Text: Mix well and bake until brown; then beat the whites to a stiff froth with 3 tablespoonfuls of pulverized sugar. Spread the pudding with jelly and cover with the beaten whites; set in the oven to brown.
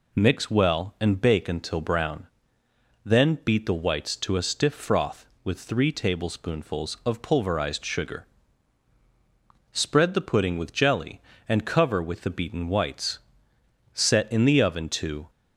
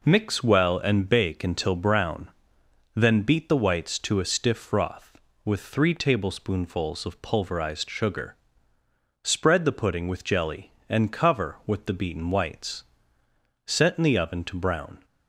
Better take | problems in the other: second | stops before "brown"; at 15.2 s

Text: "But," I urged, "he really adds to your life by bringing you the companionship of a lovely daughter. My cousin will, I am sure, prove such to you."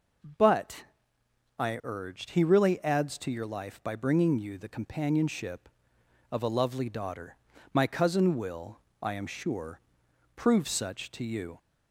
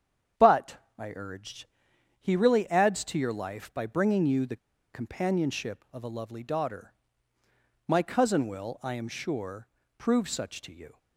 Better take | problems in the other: first | starts louder than the rest; strong; until 1.6 s; 8.5 dB // pauses between "the" and "companionship"; at 4.5 s; 0.36 s long

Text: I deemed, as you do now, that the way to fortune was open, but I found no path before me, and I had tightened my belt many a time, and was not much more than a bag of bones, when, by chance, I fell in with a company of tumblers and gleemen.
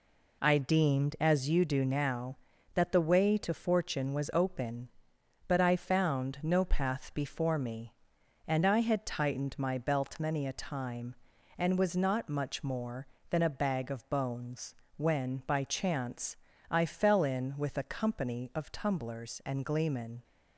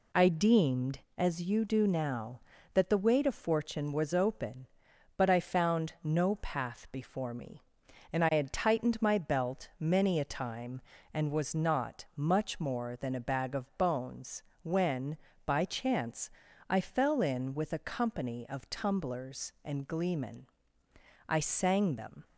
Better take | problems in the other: first | goes on to say "I sang them"; noticeable; from 21.2 s on; 0.98 s long

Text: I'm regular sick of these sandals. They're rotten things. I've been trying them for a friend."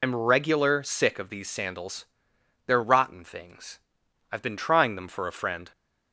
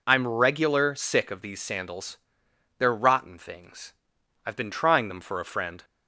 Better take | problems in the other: second | loses the start of "I'm"; at 0.0 s; 95 ms

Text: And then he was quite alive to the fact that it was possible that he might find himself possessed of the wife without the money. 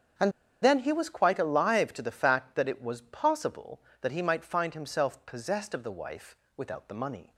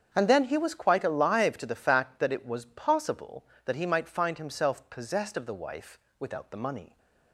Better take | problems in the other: second | starts louder than the rest; strong; until 1.4 s; 8 dB; strong in the second // pauses between "And" and "then"; slight; at 0.3 s; 0.30 s long // pauses between "wife" and "without"; slight; at 6.3 s; 0.20 s long; slight in the second

